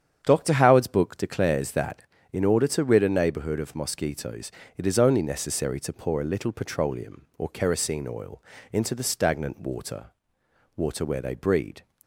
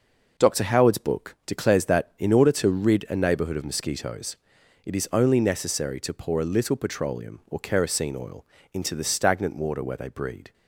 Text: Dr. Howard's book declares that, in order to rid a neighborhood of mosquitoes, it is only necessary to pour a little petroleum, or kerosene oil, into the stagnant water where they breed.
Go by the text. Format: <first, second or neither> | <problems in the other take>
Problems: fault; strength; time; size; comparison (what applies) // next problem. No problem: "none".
second | starts louder than the rest; strong; until 1.2 s; 9 dB // says "water" twice; at 10.7 s